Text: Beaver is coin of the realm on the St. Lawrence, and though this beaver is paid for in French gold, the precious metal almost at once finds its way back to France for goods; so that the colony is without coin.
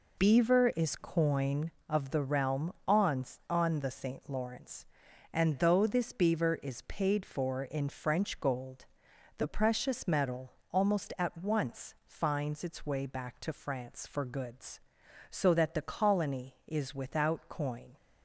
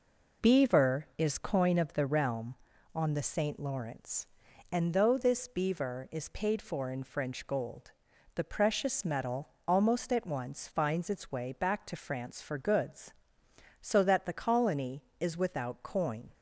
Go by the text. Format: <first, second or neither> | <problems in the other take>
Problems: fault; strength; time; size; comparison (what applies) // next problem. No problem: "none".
second | says "on" twice; at 3.4 s // pauses between "metal" and "almost"; slight; at 10.5 s; 0.18 s long; slight in the second